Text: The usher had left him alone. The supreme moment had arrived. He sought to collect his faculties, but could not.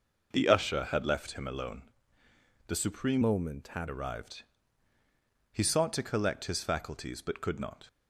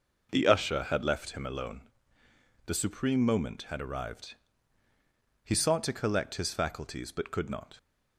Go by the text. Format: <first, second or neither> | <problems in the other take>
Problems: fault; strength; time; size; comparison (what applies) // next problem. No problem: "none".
second | changes voice from "moment" to "had"; from 3.2 to 3.8 s; 0.6 s long